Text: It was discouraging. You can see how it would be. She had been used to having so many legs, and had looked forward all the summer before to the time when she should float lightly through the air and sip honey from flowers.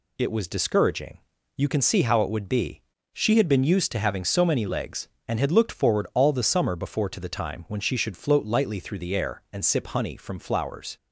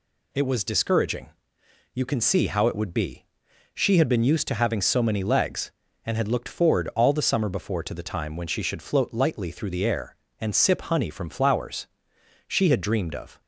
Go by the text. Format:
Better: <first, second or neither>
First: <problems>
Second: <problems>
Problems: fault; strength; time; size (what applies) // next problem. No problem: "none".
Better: first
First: none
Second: goes on to say "She had dreamed of"; noticeable; from 12.4 s on; 0.94 s long